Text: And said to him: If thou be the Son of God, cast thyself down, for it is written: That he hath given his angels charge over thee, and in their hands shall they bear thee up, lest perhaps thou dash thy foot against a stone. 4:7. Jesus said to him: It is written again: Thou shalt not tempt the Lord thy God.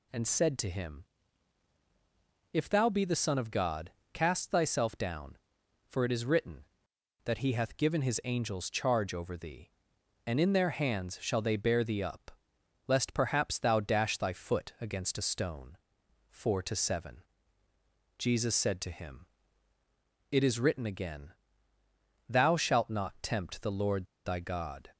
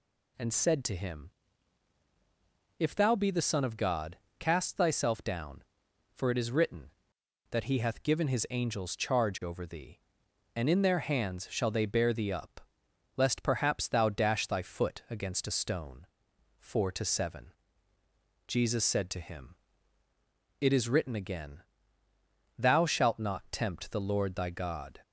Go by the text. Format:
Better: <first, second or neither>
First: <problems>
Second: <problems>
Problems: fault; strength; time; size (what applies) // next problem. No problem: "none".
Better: second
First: pauses between "Lord" and "thy"; slight; at 24.0 s; 0.19 s long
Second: none